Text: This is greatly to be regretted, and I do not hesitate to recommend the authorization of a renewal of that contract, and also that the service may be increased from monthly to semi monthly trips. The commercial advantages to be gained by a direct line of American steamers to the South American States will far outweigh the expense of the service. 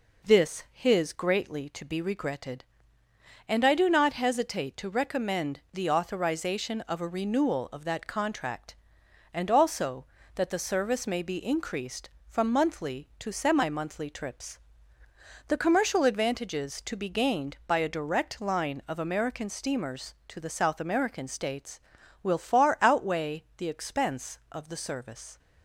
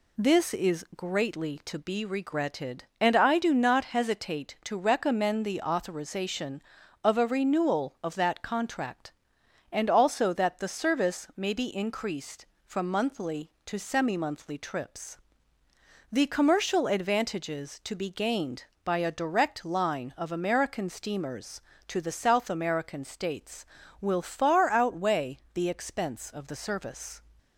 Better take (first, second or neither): second